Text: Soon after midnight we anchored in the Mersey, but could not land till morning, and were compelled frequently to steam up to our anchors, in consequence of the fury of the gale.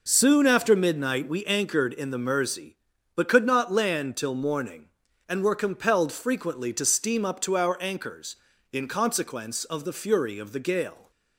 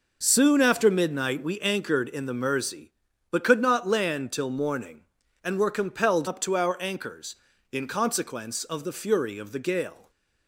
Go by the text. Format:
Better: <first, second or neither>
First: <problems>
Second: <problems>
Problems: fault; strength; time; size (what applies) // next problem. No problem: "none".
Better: first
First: none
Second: skips "frequently to steam"; at 6.2 s // stays silent after the last word; slight; from 9.9 s on; 0.5 s long